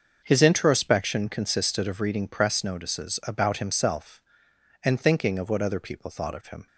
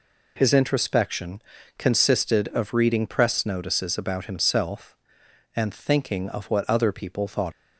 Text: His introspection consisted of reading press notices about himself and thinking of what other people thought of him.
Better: first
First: none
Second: pauses between "introspection" and "consisted"; at 1.4 s; 0.38 s long // stops before "of him"; at 7.5 s

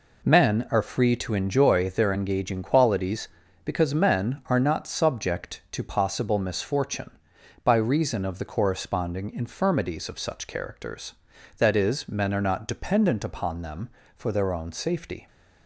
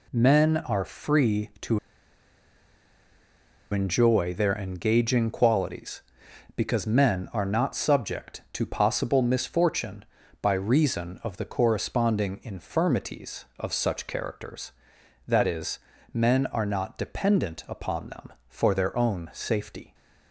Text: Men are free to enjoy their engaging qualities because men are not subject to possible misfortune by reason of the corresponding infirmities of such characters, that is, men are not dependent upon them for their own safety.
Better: first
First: none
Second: pauses between "to" and "enjoy"; strong; at 1.7 s; 1.9 s long

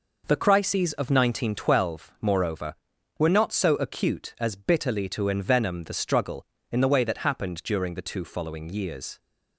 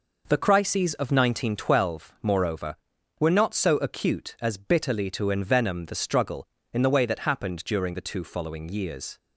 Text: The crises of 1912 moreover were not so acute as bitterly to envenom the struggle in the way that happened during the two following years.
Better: neither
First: none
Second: none

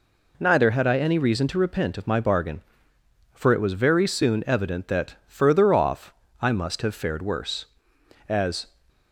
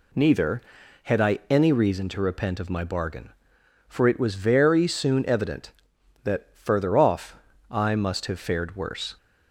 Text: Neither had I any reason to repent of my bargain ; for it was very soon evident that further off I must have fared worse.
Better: second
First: pauses between "off" and "I"; slight; at 6.1 s; 0.30 s long // goes on to say "As"; slight; from 8.2 s on; 0.38 s long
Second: pauses between "off" and "I"; slight; at 7.3 s; 0.34 s long

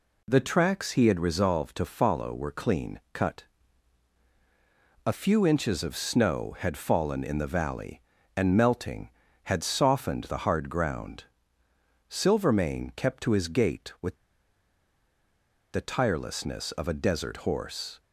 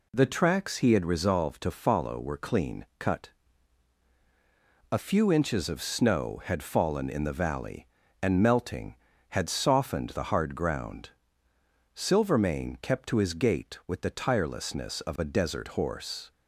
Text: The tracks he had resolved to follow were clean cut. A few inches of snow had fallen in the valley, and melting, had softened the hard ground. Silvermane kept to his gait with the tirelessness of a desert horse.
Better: second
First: pauses between "with" and "the"; strong; at 14.1 s; 1.5 s long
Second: none

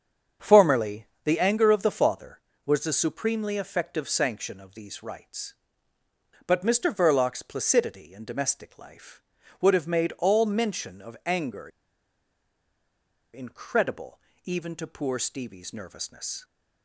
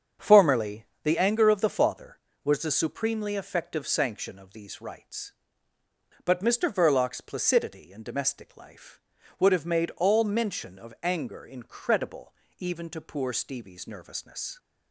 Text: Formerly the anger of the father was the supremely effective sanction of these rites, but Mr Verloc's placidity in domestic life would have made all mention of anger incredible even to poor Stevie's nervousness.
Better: second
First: starts louder than the rest; strong; until 1.5 s; 7.5 dB // pauses between "Formerly" and "the"; slight; at 1.0 s; 0.18 s long // pauses between "anger" and "incredible"; strong; at 11.6 s; 1.6 s long // pauses between "incredible" and "even"; slight; at 14.1 s; 0.24 s long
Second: starts louder than the rest; strong; until 1.3 s; 7.5 dB // pauses between "Formerly" and "the"; slight; at 0.8 s; 0.18 s long // pauses between "incredible" and "even"; slight; at 12.3 s; 0.24 s long

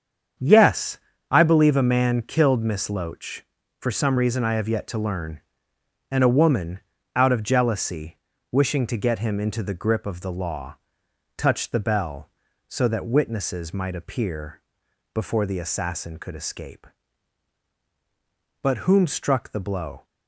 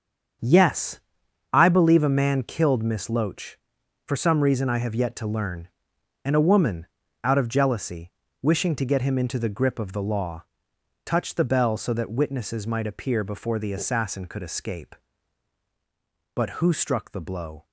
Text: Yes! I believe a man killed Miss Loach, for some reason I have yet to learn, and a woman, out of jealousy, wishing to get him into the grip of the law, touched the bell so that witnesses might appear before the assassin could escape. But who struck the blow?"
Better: second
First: starts louder than the rest; strong; until 1.7 s; 7.5 dB // pauses between "appear" and "before"; noticeable; at 14.6 s; 0.54 s long // says "whom" for "who"; at 18.7 s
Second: starts louder than the rest; strong; until 1.9 s; 7 dB

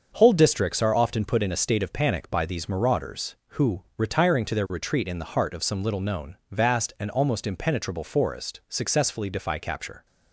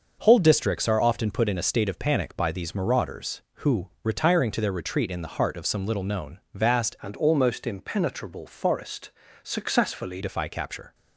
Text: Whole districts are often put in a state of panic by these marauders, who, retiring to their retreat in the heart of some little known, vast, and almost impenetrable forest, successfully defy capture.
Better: first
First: starts louder than the rest; until 1.1 s; 6.5 dB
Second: starts louder than the rest; until 1.2 s; 6 dB // changes voice from "and" to "successfully"; from 7.0 to 10.2 s; 3.2 s long

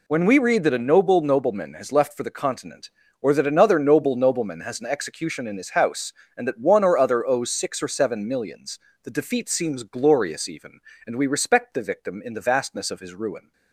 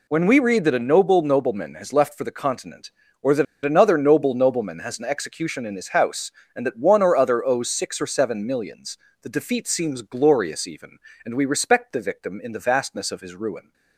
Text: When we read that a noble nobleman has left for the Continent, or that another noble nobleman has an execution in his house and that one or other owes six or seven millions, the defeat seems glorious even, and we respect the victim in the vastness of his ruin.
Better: first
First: none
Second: pauses between "that" and "another"; slight; at 3.4 s; 0.19 s long

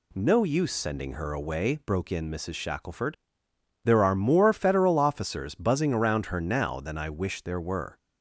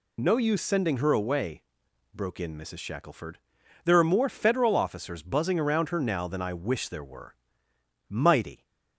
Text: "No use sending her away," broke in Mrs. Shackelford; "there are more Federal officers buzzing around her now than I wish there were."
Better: first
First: none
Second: goes on to say "Mighty"; from 8.0 s on; 0.56 s long

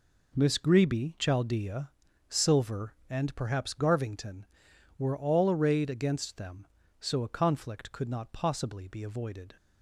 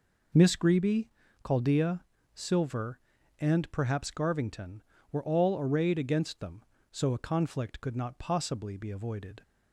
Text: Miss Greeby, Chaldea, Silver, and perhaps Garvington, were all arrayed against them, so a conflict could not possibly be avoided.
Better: neither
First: none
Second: none

